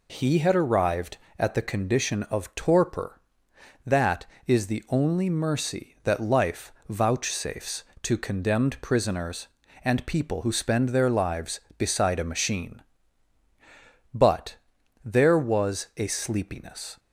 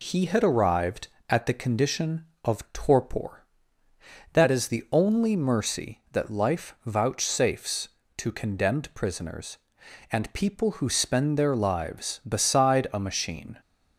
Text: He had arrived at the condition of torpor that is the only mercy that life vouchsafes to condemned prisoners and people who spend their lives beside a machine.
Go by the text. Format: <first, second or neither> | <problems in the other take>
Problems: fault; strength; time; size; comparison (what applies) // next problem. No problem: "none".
second | pauses between "life" and "vouchsafes"; slight; at 6.7 s; 0.16 s long // goes on to say "But there was a sleepiness"; strong; from 14.1 s on; 2.8 s long